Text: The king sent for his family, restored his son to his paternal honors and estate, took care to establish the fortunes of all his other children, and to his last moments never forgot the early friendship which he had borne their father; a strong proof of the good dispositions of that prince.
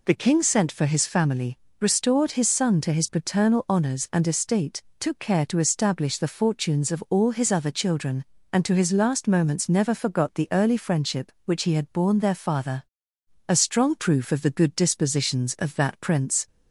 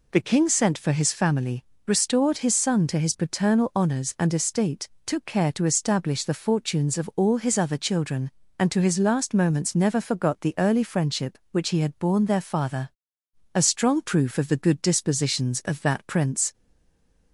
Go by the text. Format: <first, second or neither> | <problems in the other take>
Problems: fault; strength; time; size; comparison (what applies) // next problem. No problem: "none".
first | stays silent after the last word; slight; from 16.5 s on; 0.8 s long